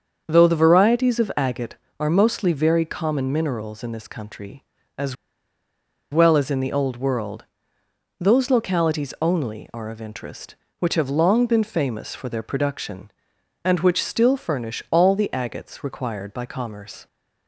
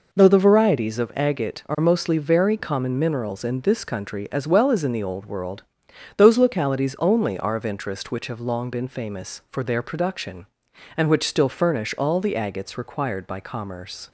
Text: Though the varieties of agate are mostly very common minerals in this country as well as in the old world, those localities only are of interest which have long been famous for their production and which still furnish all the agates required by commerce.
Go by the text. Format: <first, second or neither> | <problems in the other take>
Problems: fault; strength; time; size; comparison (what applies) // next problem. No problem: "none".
second | starts louder than the rest; until 1.2 s; 7 dB // pauses between "as" and "well"; noticeable; at 5.1 s; 0.97 s long